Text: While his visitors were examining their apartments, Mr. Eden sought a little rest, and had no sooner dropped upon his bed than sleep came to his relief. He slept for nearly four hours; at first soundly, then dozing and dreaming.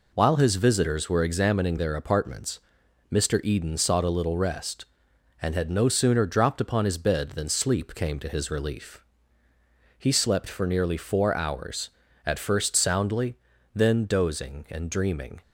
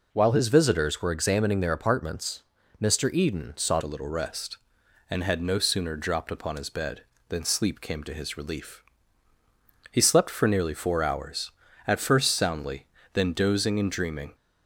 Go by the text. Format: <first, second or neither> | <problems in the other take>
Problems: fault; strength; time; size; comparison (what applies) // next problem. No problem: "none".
first | changes voice at "a"; from 3.8 s on; 10.5 s long